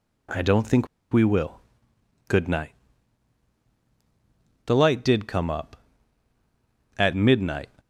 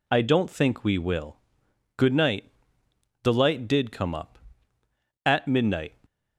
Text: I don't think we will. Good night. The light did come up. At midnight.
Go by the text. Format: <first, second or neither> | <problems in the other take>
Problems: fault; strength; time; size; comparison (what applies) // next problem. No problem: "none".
second | pauses between "think" and "we"; slight; at 0.8 s; 0.24 s long